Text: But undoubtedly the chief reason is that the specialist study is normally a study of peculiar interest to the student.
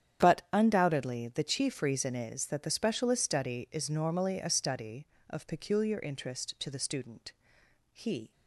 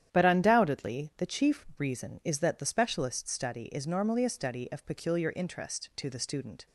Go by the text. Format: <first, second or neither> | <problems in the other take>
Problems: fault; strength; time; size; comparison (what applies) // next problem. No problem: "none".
second | starts louder than the rest; strong; until 1.3 s; 9 dB; strong in the second // goes on to say "He"; slight; from 7.9 s on; 0.40 s long